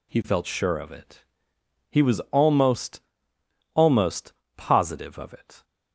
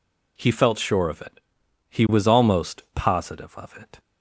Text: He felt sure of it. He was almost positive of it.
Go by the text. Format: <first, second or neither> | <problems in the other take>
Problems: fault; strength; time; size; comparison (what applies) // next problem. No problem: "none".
second | says "almost" twice; at 3.7 s